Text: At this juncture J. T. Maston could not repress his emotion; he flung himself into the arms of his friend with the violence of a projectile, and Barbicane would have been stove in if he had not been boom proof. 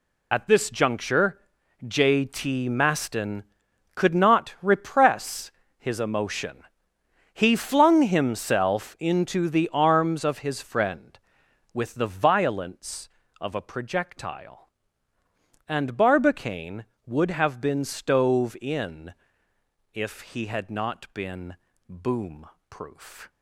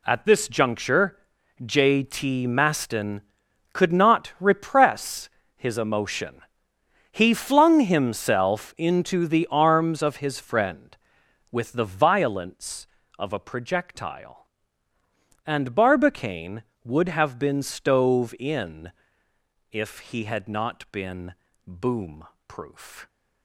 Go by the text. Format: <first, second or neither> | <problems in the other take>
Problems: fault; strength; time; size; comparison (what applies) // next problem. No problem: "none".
second | loses the start of "At"; at 0.3 s; 45 ms // pauses between "juncture" and "J"; noticeable; at 1.4 s; 0.46 s long; noticeable in the second // pauses between "repress" and "his"; slight; at 5.5 s; 0.26 s long; slight in the second // pauses between "in" and "if"; noticeable; at 19.1 s; 0.80 s long; noticeable in the second // pauses between "been" and "boom"; slight; at 21.5 s; 0.32 s long; slight in the second // pauses between "boom" and "proof"; slight; at 22.4 s; 0.22 s long; slight in the second